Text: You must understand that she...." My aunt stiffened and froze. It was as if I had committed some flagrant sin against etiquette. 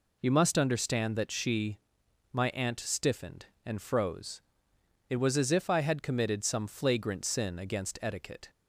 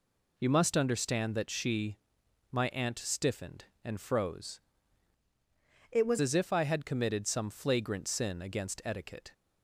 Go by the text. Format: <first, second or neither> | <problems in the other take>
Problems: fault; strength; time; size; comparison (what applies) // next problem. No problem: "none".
first | changes voice from "It" to "was"; from 5.9 to 6.1 s; 0.2 s long